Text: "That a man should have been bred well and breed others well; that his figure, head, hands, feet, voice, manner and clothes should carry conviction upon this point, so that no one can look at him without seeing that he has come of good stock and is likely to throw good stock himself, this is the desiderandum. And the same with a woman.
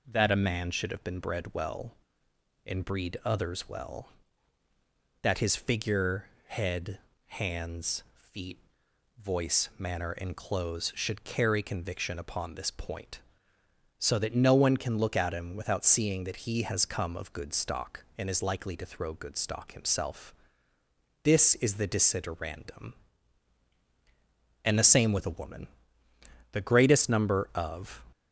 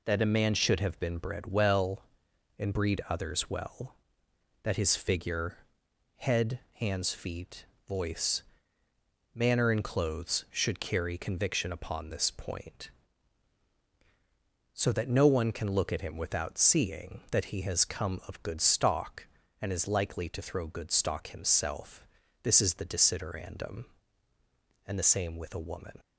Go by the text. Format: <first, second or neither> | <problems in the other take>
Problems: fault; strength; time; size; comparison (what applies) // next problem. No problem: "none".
second | goes on to say "The greatest number of"; from 26.5 s on; 1.5 s long